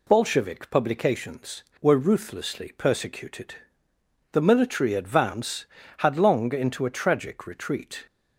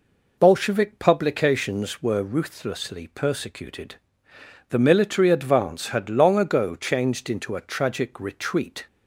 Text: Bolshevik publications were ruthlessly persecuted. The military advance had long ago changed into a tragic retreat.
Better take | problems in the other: second | skips "ago changed"; at 6.5 s

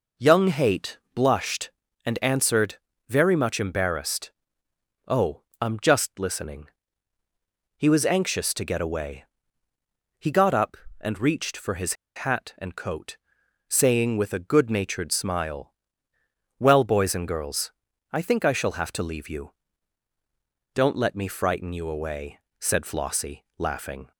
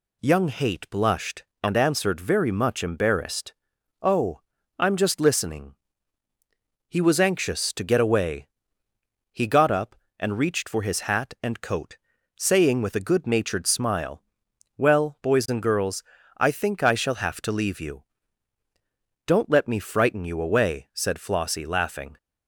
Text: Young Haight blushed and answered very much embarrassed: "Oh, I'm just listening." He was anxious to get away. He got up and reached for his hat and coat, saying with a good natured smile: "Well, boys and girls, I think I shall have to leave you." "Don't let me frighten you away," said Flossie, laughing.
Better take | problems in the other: second | pauses between "Haight" and "blushed"; slight; at 0.9 s; 0.16 s long // pauses between "answered" and "very"; slight; at 2.7 s; 0.30 s long // pauses between "his" and "hat"; slight; at 11.9 s; 0.22 s long

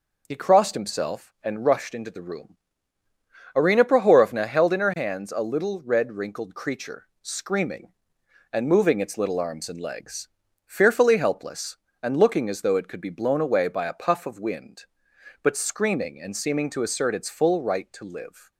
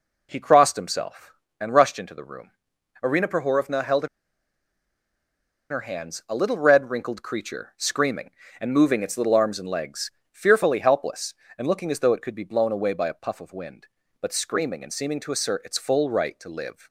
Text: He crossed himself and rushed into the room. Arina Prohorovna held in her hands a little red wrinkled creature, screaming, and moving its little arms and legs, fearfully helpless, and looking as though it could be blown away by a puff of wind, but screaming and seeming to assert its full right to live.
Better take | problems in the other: first | pauses between "in" and "her"; strong; at 4.0 s; 1.6 s long

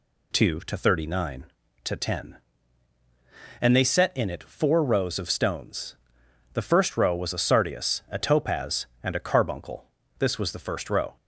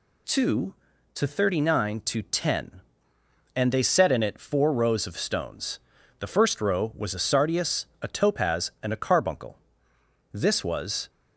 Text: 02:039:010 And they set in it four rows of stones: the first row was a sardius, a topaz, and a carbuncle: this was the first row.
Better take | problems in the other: first | stops before "the first row"; at 11.0 s

